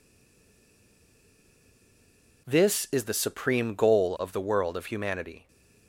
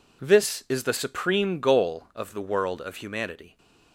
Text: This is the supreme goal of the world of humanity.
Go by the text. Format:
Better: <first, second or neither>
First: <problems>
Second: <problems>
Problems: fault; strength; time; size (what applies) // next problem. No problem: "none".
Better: second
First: stays silent before the first word; until 2.4 s; 2.4 s long // stays silent after the last word; slight; from 5.3 s on; 0.5 s long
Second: none